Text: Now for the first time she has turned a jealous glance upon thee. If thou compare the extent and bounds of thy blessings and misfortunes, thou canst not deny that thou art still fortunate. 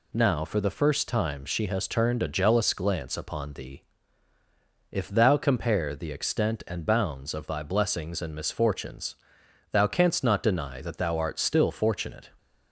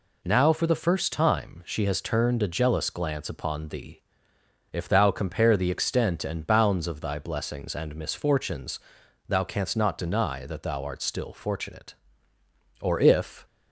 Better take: first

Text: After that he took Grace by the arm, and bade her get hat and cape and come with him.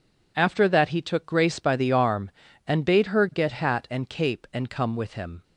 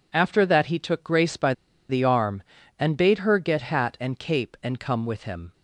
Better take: first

